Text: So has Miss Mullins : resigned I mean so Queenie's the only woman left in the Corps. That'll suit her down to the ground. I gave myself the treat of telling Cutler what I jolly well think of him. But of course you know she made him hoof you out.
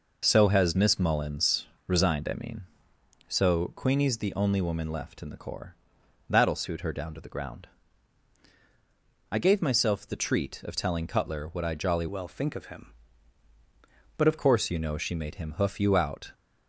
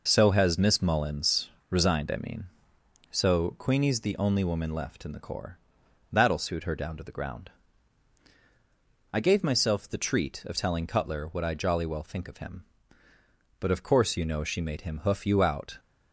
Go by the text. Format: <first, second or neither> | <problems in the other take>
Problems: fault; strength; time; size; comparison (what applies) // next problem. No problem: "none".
second | changes voice from "well" to "of"; from 12.0 to 14.3 s; 2.3 s long